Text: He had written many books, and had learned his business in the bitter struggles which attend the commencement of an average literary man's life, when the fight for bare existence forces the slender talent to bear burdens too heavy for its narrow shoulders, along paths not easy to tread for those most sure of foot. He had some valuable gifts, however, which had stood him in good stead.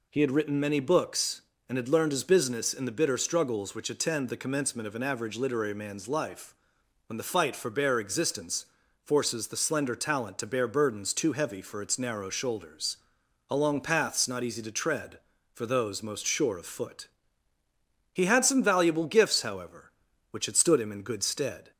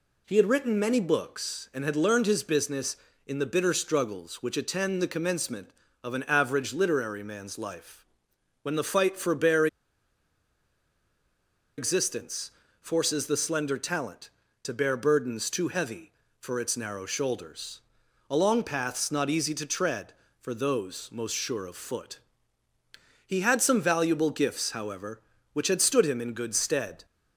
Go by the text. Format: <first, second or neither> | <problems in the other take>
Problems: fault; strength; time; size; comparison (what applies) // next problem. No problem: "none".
first | pauses between "bare" and "existence"; strong; at 9.6 s; 2.1 s long // pauses between "existence" and "forces"; slight; at 12.4 s; 0.32 s long; also in the first